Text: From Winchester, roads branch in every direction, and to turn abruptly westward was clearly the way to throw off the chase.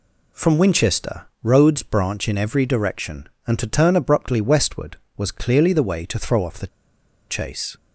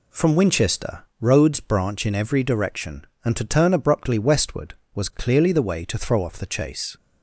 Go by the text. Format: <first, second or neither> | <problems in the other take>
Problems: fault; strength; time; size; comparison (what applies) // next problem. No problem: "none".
second | pauses between "the" and "chase"; noticeable; at 6.6 s; 0.62 s long